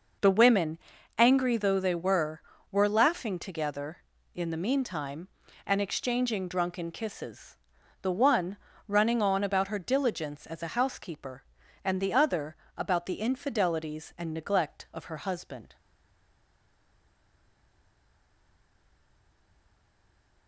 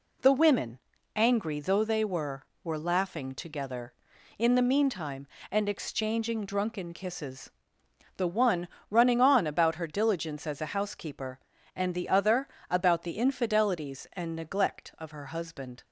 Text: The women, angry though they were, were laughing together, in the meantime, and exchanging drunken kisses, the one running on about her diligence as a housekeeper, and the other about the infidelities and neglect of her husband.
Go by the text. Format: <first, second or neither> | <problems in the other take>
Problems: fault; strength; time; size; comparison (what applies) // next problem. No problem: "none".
second | pauses between "one" and "running"; slight; at 8.5 s; 0.32 s long; slight in the second // pauses between "other" and "about"; slight; at 12.5 s; 0.20 s long; slight in the second // stays silent after the last word; strong; from 15.7 s on; 4.7 s long